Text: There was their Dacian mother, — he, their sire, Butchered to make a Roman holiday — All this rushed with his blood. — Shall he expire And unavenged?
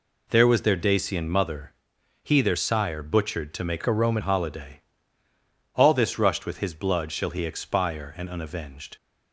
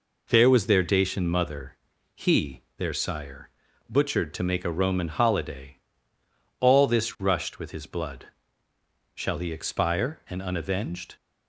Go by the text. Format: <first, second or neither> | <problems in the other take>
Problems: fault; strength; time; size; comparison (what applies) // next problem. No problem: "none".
second | changes voice from "a" to "Roman"; from 3.8 to 4.2 s; 0.4 s long